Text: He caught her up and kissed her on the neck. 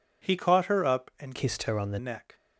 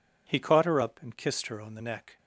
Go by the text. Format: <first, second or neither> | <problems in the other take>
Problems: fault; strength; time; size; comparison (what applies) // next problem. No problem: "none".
second | changes voice from "kissed" to "the"; from 1.3 to 1.9 s; 0.6 s long